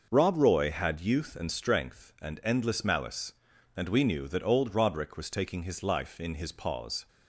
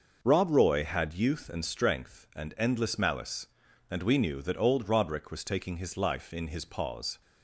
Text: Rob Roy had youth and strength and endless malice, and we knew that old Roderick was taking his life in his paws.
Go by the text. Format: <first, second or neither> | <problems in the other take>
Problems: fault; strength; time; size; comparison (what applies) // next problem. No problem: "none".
neither | none